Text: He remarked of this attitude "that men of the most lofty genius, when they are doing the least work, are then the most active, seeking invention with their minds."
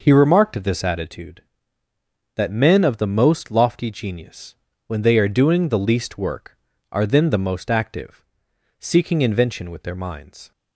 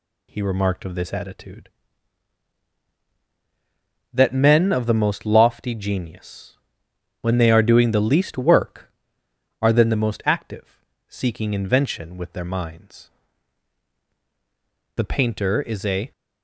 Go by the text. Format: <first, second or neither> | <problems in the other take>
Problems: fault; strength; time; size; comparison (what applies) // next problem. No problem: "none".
first | goes on to say "The painter is a"; noticeable; from 14.9 s on; 1.1 s long